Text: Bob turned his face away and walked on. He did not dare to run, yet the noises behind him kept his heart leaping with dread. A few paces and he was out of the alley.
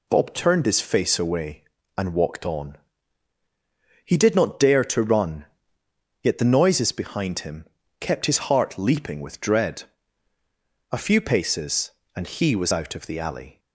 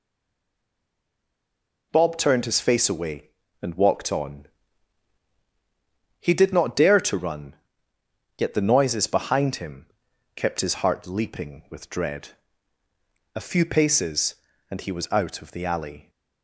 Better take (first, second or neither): first